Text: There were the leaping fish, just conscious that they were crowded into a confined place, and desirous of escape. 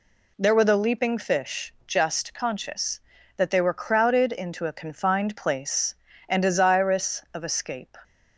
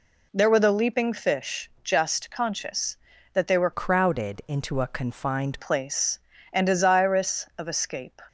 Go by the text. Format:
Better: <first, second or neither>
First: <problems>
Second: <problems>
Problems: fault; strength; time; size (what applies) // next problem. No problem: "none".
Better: first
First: none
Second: changes voice from "crowded" to "confined"; from 3.7 to 5.5 s; 1.8 s long